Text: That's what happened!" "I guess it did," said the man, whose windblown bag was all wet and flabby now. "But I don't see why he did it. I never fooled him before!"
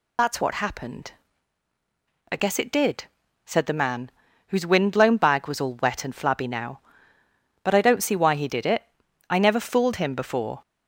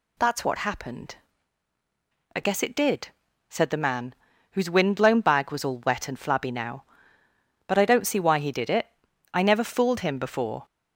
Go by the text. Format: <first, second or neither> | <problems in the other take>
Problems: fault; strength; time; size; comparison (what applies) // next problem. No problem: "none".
second | loses the start of "That's"; at 0.1 s; 40 ms